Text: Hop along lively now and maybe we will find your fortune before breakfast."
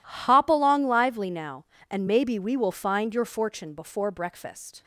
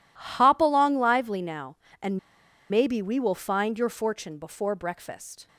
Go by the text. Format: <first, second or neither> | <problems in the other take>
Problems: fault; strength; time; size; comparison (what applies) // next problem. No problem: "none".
first | pauses between "and" and "maybe"; noticeable; at 2.1 s; 0.51 s long